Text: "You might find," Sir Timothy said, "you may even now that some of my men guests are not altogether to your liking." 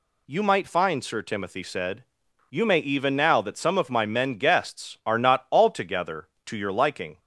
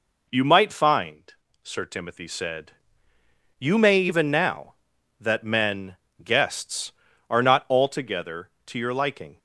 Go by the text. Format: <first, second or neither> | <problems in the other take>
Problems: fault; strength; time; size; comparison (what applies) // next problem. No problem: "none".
first | skips "some of my"; at 5.4 s // pauses between "men" and "guests"; slight; at 5.9 s; 0.26 s long